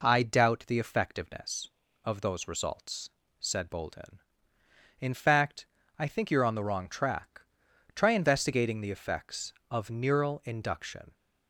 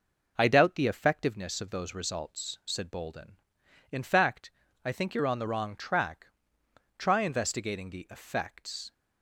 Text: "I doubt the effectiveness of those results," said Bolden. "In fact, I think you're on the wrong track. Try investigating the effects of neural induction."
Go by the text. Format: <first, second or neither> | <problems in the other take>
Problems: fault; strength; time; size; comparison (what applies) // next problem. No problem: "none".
first | stops before "of neural induction"; at 8.9 s